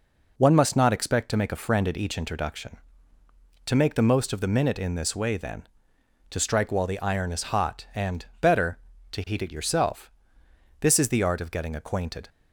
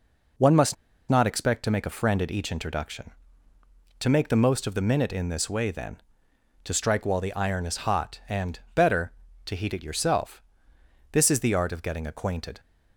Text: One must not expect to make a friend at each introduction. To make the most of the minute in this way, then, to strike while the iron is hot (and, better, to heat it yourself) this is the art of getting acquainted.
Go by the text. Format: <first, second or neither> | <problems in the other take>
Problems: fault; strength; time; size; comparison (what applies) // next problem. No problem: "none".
first | pauses between "must" and "not"; slight; at 0.7 s; 0.34 s long